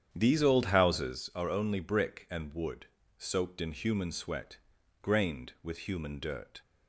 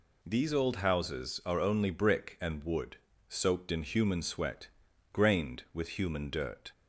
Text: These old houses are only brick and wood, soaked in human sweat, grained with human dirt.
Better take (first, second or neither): second